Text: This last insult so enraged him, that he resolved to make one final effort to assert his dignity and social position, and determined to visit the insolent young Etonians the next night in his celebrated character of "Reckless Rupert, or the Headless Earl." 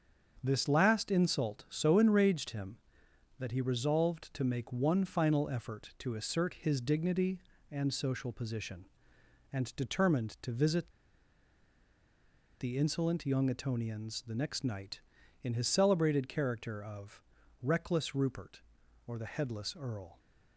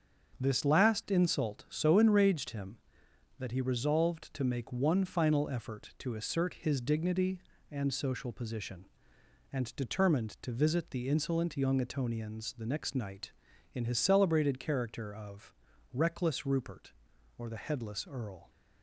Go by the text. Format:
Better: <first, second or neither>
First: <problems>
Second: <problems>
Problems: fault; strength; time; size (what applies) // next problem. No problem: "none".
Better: second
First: starts louder than the rest; until 1.4 s; 7 dB // pauses between "visit" and "the"; strong; at 10.8 s; 1.7 s long // pauses between "of" and "Reckless"; at 17.2 s; 0.40 s long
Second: starts louder than the rest; until 1.4 s; 7 dB // pauses between "of" and "Reckless"; at 15.5 s; 0.40 s long